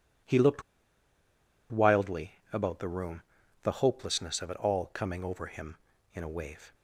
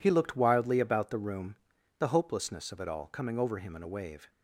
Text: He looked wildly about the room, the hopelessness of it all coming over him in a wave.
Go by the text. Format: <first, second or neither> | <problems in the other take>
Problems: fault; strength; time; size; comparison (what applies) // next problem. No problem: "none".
second | pauses between "looked" and "wildly"; at 0.6 s; 1.0 s long